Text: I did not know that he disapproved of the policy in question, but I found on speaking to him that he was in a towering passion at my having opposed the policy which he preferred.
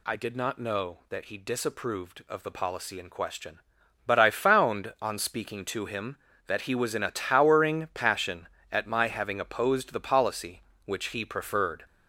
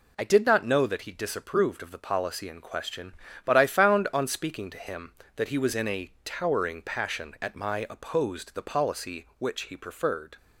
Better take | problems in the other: first | skips "having"; at 7.8 s

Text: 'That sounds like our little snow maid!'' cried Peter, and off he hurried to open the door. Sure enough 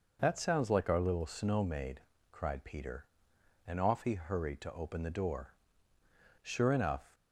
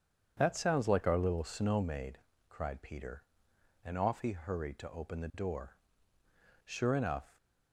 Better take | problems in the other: first | starts louder than the rest; strong; until 2.1 s; 7.5 dB

